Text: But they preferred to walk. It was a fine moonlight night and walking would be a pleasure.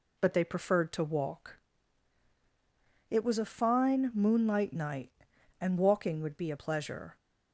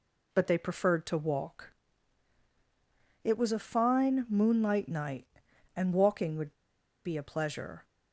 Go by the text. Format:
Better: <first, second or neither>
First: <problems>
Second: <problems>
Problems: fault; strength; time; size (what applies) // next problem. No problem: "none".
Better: first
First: none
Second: pauses between "would" and "be"; noticeable; at 6.5 s; 0.52 s long